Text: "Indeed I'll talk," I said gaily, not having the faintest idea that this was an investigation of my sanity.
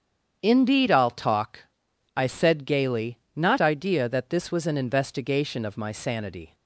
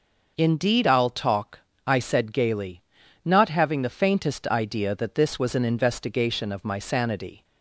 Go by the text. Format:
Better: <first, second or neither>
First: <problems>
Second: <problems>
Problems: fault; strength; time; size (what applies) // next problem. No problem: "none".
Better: second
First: starts louder than the rest; strong; until 1.4 s; 8 dB // skips "having the faintest"; at 3.5 s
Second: none